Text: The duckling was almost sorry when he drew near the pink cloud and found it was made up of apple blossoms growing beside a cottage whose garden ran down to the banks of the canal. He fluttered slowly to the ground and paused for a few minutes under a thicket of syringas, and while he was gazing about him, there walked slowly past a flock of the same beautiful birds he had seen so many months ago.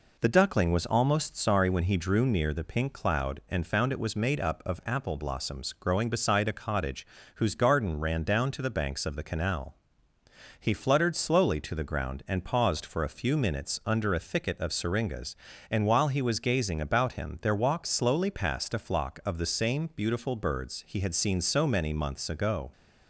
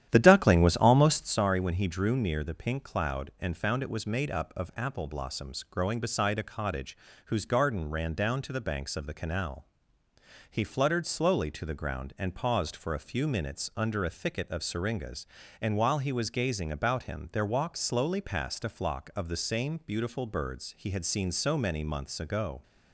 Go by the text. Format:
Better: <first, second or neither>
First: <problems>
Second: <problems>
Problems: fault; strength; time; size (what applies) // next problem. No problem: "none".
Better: first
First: pauses between "cottage" and "whose"; slight; at 7.0 s; 0.30 s long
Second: starts louder than the rest; strong; until 1.4 s; 11 dB // pauses between "cottage" and "whose"; slight; at 6.9 s; 0.30 s long